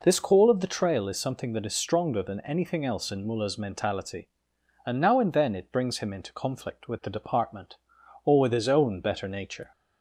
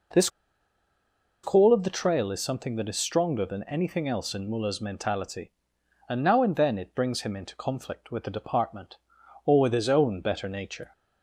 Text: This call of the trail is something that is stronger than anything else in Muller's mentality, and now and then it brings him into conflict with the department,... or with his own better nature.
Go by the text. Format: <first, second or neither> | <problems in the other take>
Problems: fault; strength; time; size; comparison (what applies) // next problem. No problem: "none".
first | pauses between "This" and "call"; at 0.2 s; 1.1 s long